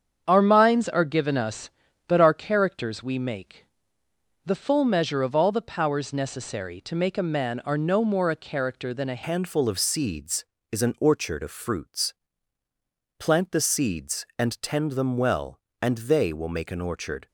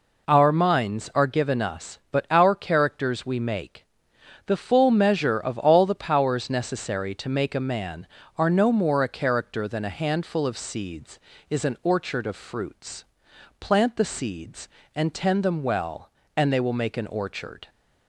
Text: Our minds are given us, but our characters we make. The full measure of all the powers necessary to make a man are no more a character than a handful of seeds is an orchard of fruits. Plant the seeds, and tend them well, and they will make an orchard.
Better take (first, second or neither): second